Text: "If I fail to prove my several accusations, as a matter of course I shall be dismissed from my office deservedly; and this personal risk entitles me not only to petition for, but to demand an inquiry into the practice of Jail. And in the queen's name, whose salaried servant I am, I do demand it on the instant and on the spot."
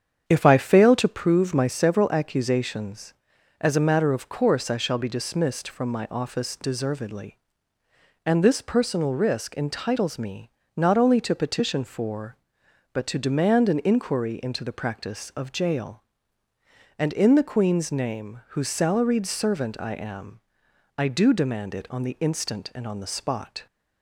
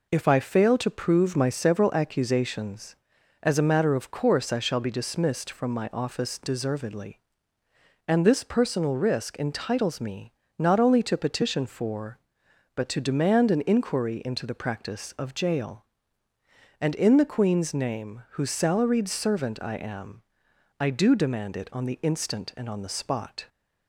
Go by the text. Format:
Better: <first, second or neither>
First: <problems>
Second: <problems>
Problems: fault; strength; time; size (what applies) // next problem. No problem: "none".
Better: second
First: starts louder than the rest; strong; until 1.2 s; 8 dB // pauses between "me" and "not"; slight; at 10.5 s; 0.26 s long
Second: pauses between "me" and "not"; slight; at 10.3 s; 0.26 s long